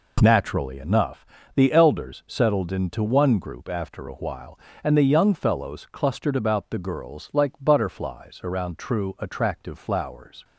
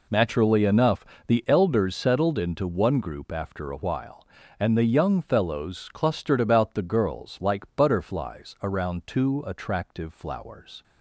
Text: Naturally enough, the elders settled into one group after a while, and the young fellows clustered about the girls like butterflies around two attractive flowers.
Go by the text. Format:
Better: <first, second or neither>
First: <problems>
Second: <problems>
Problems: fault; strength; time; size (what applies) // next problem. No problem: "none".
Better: second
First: says "true" for "two"; at 8.7 s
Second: none